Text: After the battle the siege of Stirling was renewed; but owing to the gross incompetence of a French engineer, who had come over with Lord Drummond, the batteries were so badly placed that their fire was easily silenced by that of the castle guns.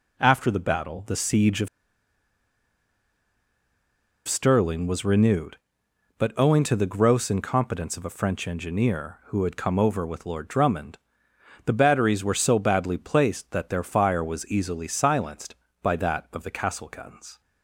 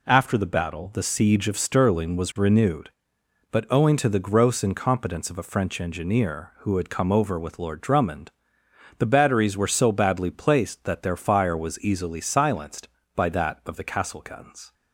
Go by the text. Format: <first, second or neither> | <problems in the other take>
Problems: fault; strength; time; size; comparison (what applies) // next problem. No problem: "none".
second | pauses between "of" and "Stirling"; strong; at 1.6 s; 2.5 s long